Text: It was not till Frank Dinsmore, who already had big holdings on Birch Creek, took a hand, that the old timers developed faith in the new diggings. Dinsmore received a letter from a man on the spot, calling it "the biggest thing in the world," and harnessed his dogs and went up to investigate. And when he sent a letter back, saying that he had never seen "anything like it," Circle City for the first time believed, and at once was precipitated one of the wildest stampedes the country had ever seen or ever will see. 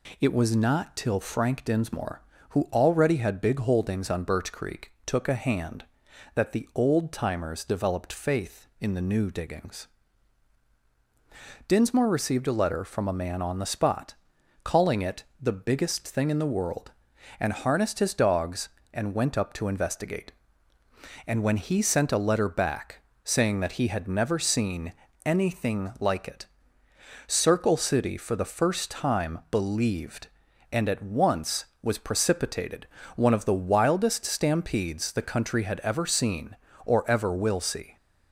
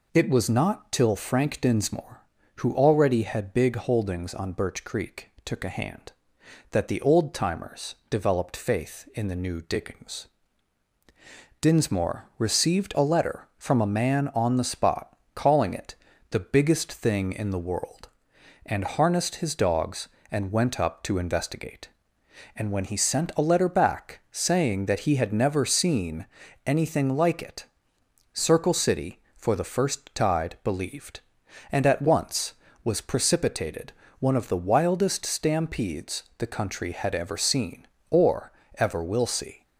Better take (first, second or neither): first